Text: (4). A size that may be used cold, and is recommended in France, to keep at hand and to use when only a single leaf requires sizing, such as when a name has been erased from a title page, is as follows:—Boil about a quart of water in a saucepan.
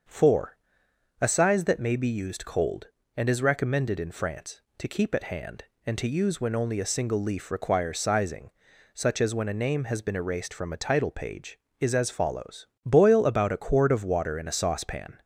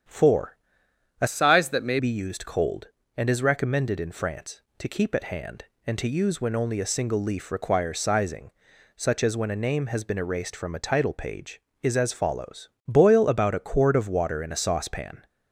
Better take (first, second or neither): first